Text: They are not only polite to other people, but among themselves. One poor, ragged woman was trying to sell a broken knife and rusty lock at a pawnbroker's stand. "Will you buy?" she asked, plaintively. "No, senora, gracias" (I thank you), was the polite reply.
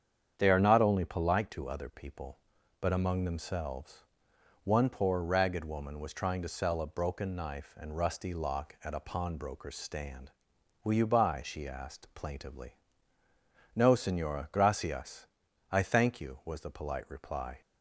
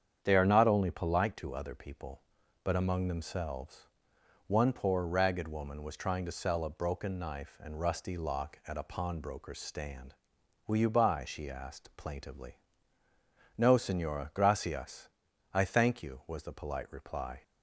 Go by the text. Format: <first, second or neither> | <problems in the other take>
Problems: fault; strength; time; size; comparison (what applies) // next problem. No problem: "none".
neither | starts louder than the rest; strong; the same in both